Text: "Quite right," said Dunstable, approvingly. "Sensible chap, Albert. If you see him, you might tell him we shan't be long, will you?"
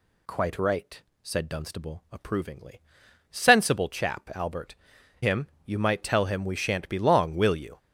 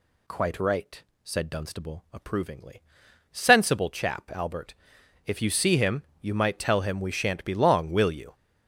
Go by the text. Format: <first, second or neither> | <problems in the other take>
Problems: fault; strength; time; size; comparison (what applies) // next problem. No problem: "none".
second | skips "If you see"; at 4.9 s